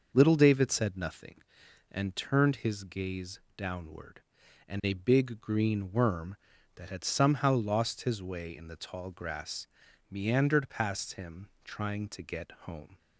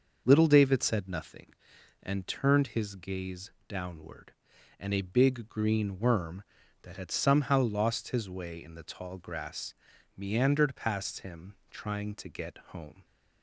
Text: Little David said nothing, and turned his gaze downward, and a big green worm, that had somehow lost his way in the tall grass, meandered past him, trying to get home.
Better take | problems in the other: neither | starts louder than the rest; noticeable; the same in both // pauses between "gaze" and "downward"; slight; the same in both

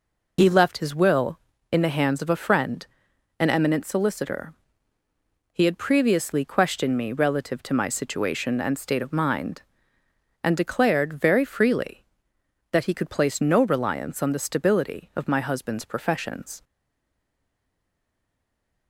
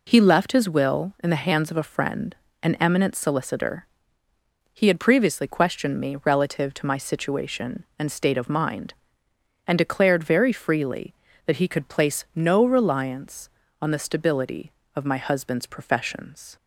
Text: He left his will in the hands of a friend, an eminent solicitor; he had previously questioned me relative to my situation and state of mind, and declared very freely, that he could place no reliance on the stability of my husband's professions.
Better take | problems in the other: second | stays silent after the last word; from 16.6 s on; 2.2 s long

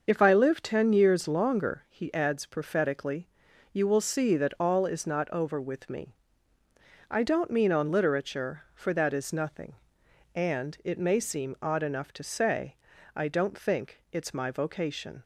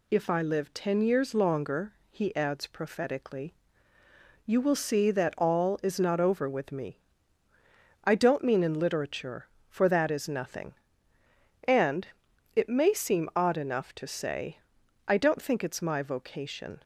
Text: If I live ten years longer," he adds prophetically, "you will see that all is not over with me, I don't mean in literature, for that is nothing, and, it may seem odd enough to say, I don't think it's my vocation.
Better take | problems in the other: second | starts louder than the rest; until 1.0 s; 6.5 dB // says "on" for "in"; at 7.7 s

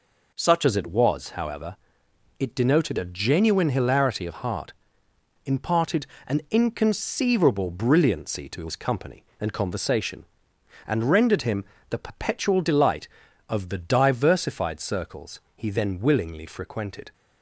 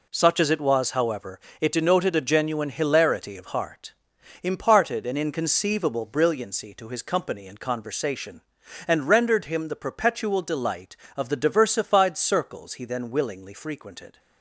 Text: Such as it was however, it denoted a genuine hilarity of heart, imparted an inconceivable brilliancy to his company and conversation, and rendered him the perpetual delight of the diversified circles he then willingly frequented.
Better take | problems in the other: second | changes voice at "as"; from 0.6 s on; 16.5 s long // pauses between "imparted" and "an"; slight; at 6.0 s; 0.20 s long // pauses between "him" and "the"; slight; at 11.6 s; 0.28 s long // pauses between "circles" and "he"; slight; at 15.3 s; 0.16 s long

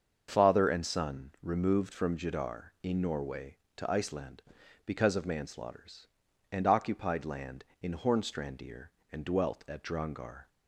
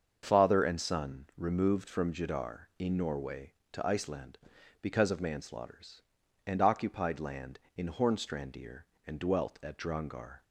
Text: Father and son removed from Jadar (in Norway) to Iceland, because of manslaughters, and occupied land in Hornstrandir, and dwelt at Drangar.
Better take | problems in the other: neither | starts louder than the rest; the same in both

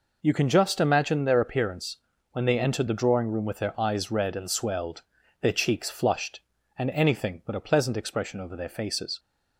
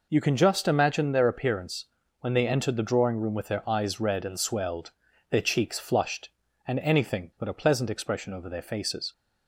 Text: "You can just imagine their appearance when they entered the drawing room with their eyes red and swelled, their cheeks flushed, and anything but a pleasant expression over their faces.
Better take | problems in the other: neither | pauses between "appearance" and "when"; slight; the same in both

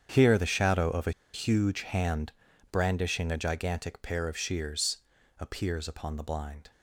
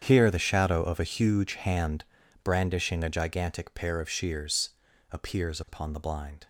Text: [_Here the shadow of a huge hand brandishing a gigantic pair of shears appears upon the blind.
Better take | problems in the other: second | starts louder than the rest; strong; until 1.1 s; 8 dB; strong in the second // pauses between "a" and "huge"; slight; at 1.1 s; 0.21 s long // pauses between "hand" and "brandishing"; at 2.3 s; 0.40 s long; also in the second // pauses between "shears" and "appears"; at 4.9 s; 0.42 s long; also in the second

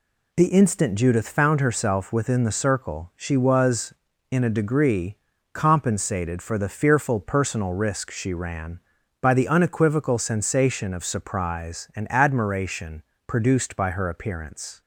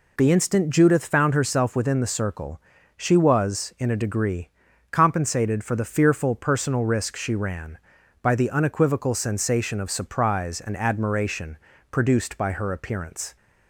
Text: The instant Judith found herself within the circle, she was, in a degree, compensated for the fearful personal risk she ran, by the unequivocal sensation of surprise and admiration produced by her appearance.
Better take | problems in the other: neither | pauses between "admiration" and "produced"; slight; the same in both

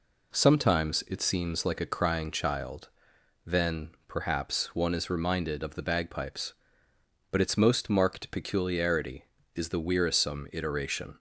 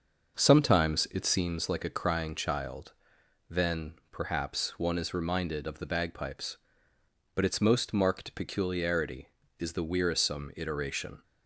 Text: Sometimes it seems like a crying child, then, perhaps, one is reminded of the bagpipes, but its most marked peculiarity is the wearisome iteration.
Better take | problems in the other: first | starts louder than the rest; noticeable; until 1.6 s; 6 dB

